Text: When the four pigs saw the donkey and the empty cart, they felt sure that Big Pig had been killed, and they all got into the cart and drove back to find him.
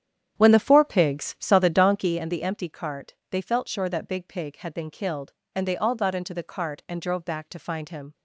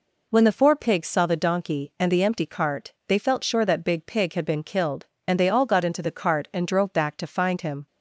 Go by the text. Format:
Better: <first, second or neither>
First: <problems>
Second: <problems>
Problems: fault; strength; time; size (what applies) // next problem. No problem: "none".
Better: second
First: starts louder than the rest; strong; until 2.3 s; 9.5 dB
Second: none